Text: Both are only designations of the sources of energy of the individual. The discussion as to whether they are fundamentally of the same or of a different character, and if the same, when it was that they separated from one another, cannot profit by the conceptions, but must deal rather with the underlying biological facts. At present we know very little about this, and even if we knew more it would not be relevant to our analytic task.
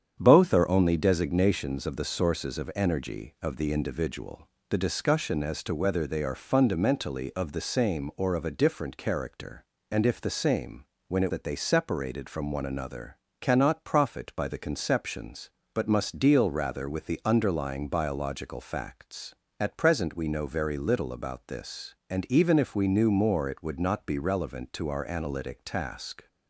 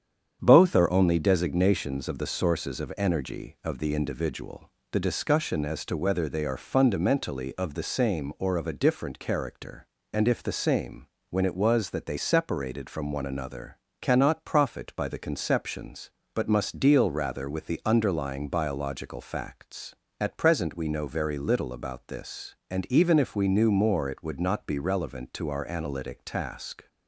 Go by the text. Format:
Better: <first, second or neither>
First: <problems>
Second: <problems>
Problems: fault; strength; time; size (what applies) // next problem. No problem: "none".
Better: second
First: starts louder than the rest; strong; until 1.2 s; 8.5 dB // skips "was"; at 11.3 s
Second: starts louder than the rest; strong; until 1.4 s; 8.5 dB